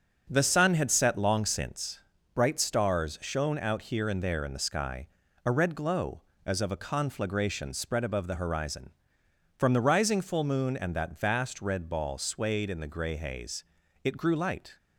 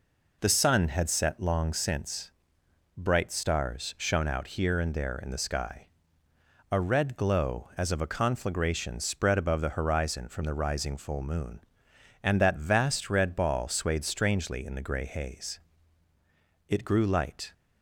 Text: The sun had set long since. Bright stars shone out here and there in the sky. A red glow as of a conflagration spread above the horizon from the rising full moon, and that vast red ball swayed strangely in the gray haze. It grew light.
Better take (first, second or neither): second